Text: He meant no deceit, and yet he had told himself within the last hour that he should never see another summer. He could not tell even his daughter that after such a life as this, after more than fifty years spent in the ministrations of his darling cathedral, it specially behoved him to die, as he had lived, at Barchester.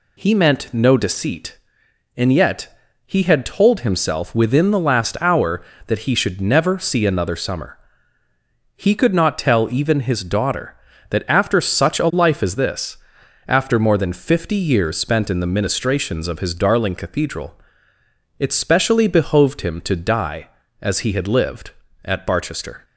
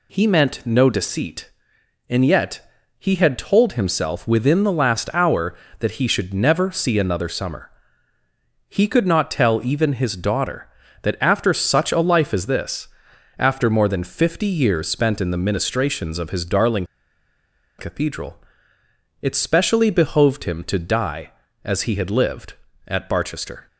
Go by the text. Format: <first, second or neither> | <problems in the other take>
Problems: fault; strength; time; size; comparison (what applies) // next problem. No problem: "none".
first | pauses between "yet" and "he"; slight; at 2.6 s; 0.30 s long; slight in the first // pauses between "darling" and "cathedral"; noticeable; at 16.8 s; 0.92 s long